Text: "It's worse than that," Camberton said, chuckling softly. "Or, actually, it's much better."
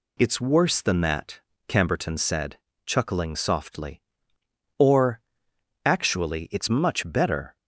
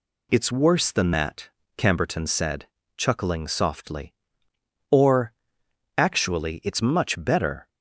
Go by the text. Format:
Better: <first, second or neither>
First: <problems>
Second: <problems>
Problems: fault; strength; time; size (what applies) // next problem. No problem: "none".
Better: neither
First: none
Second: none